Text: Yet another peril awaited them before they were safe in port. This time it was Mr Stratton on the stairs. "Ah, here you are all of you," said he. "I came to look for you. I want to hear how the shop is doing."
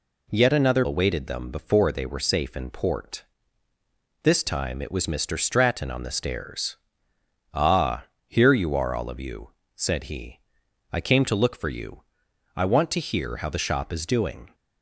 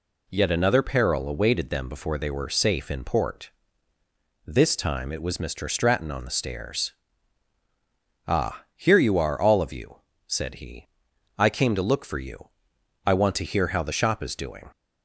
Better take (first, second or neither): second